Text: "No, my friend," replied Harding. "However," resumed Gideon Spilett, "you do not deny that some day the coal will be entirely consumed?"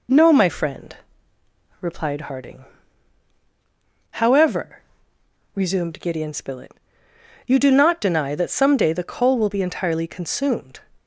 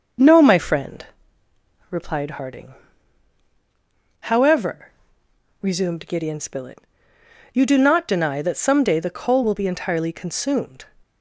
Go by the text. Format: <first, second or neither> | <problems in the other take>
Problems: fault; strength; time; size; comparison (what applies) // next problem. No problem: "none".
first | starts louder than the rest; noticeable; until 1.1 s; 6 dB